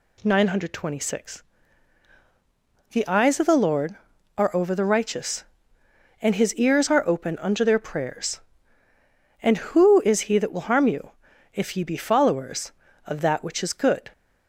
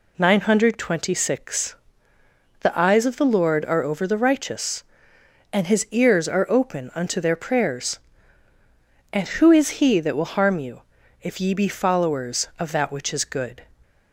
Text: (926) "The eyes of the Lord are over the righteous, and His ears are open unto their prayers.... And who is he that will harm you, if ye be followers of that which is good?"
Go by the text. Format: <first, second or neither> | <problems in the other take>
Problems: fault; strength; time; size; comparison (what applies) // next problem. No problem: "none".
neither | none